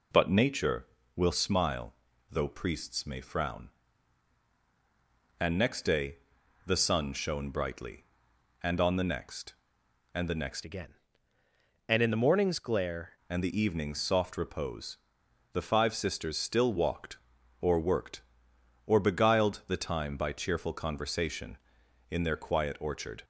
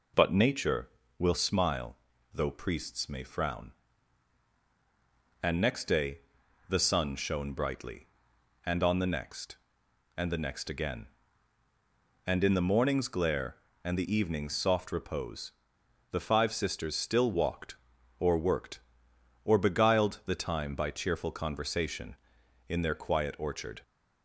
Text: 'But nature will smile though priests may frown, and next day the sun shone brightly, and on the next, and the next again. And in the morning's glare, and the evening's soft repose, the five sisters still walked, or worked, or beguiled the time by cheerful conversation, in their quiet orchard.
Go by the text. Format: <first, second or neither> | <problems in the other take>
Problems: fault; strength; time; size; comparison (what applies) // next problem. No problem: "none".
second | pauses between "smile" and "though"; slight; at 1.9 s; 0.36 s long; slight in the second // pauses between "day" and "the"; noticeable; at 6.1 s; 0.48 s long; noticeable in the second // changes voice from "again" to "glare"; from 10.6 to 13.1 s; 2.5 s long